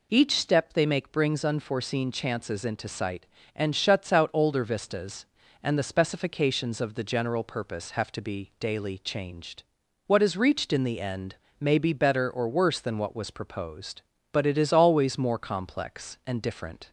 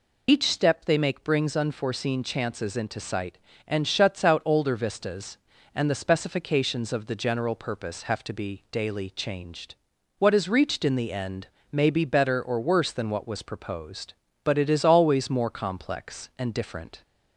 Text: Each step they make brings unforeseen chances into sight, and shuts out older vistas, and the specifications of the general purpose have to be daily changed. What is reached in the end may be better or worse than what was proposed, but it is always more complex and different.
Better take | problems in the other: first | loses the start of "Each"; at 0.2 s; 65 ms // pauses between "end" and "may"; slight; at 11.4 s; 0.22 s long; slight in the first

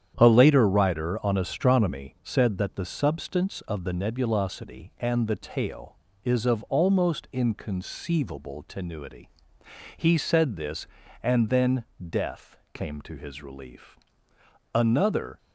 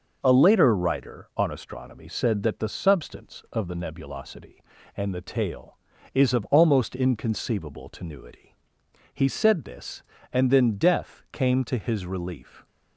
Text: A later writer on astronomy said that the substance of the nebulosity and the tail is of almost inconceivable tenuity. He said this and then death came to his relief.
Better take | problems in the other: second | starts louder than the rest; strong; until 1.1 s; 9 dB // pauses between "then" and "death"; slight; at 11.8 s; 0.24 s long // pauses between "death" and "came"; slight; at 12.5 s; 0.18 s long // goes on to say "Another"; noticeable; from 14.7 s on; 0.64 s long

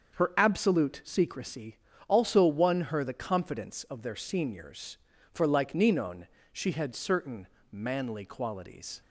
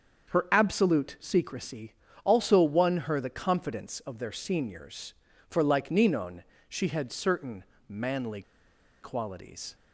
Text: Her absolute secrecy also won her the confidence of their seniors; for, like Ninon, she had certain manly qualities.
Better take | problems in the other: first | starts louder than the rest; until 1.3 s; 7 dB; also in the first // pauses between "secrecy" and "also"; slight; at 1.9 s; 0.30 s long; slight in the first // pauses between "certain" and "manly"; slight; at 7.6 s; 0.24 s long; slight in the first // pauses between "manly" and "qualities"; noticeable; at 8.4 s; 0.60 s long

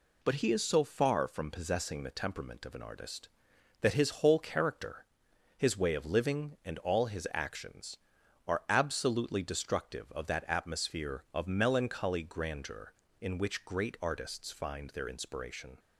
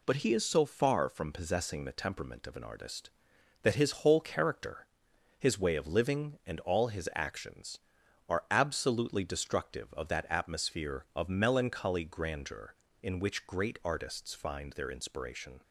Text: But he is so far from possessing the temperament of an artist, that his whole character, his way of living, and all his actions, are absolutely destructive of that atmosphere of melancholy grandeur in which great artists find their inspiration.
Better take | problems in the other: neither | none

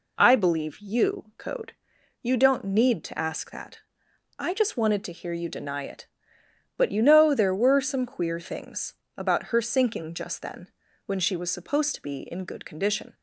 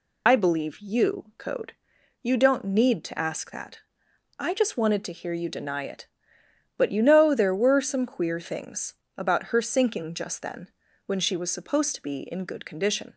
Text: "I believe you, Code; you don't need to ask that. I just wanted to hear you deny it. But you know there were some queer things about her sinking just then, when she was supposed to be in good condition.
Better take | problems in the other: first | loses the start of "I"; at 0.2 s; 75 ms // pauses between "things" and "about"; slight; at 8.9 s; 0.22 s long; slight in the first

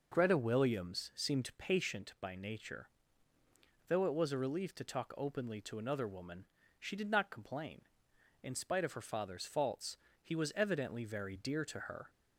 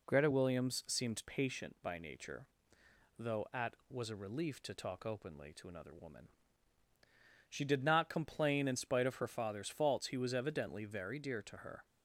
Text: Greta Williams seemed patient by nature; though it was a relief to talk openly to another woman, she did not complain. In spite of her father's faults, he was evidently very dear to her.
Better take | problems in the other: first | says "at" for "it"; at 3.5 s

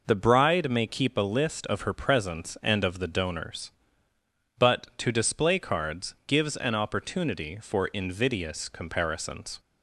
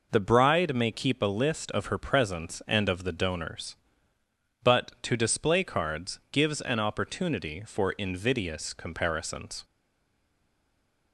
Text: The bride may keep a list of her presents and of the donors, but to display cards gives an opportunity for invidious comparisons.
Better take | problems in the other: first | stays silent after the last word; noticeable; from 9.6 s on; 1.5 s long

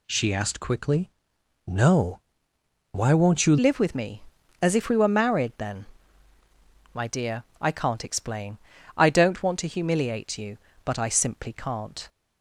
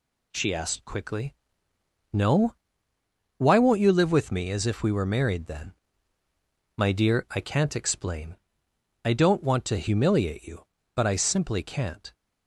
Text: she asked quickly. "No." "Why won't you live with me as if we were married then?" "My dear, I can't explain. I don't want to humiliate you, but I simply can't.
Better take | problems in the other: second | changes voice at "live"; from 3.5 s on; 8.5 s long

